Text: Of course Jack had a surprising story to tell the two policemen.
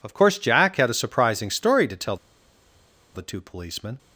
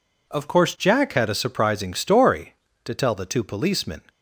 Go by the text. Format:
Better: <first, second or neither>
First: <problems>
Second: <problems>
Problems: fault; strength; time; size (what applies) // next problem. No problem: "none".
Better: second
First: pauses between "tell" and "the"; at 2.1 s; 0.99 s long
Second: none